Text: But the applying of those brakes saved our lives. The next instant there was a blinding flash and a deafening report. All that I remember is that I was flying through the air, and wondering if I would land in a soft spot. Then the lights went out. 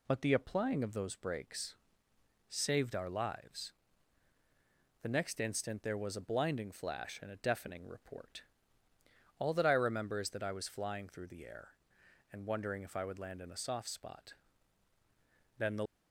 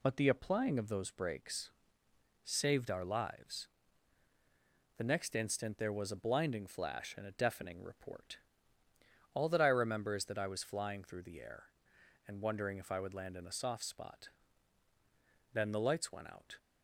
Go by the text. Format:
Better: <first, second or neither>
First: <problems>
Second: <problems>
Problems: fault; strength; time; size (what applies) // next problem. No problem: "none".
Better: second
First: pauses between "brakes" and "saved"; noticeable; at 1.7 s; 0.72 s long // stops before "lights went out"; at 15.8 s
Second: pauses between "brakes" and "saved"; noticeable; at 1.7 s; 0.72 s long